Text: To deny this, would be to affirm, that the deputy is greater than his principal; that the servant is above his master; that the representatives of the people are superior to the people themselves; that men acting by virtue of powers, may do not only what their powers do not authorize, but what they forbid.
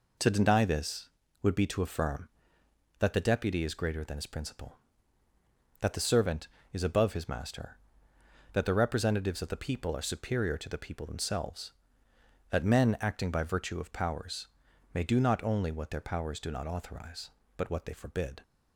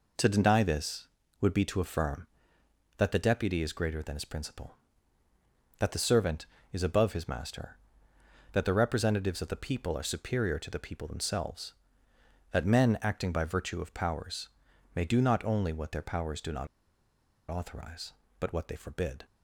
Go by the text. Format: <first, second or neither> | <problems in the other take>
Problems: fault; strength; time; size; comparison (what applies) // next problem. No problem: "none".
first | pauses between "not" and "authorize"; noticeable; at 16.6 s; 0.83 s long